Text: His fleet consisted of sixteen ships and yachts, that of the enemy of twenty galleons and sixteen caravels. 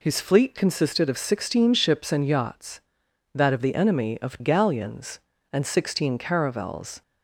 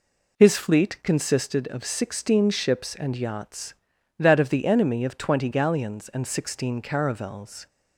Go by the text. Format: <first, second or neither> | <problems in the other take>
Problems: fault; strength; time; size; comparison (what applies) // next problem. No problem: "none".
second | skips "twenty"; at 4.3 s